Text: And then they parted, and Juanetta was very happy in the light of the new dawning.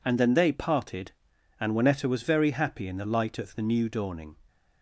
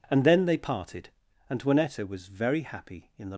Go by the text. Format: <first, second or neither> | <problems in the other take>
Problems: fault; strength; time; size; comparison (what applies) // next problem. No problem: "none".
first | stops before "light of the new dawning"; at 3.3 s